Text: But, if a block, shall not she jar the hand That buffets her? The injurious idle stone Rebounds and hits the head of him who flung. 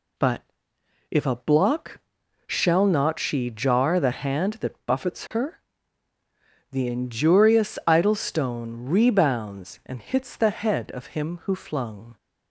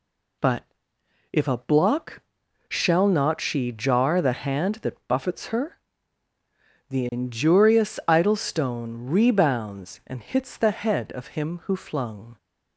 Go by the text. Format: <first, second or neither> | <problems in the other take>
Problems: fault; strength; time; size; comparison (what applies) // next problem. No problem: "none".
neither | none